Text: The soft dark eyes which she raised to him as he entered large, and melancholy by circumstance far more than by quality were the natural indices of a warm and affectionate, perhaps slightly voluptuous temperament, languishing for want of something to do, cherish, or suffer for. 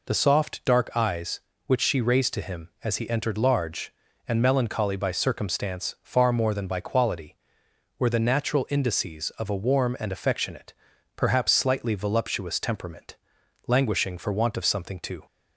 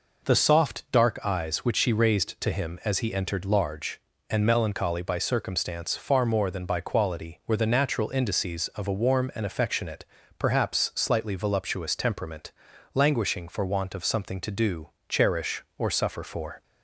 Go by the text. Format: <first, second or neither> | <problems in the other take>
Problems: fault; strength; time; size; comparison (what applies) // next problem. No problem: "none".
second | stops before "do cherish or suffer for"; at 15.2 s